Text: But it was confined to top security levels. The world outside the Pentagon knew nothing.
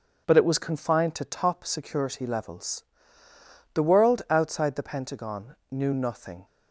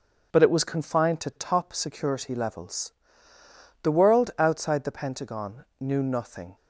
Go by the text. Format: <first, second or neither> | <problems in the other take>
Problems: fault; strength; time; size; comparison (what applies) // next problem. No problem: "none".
neither | none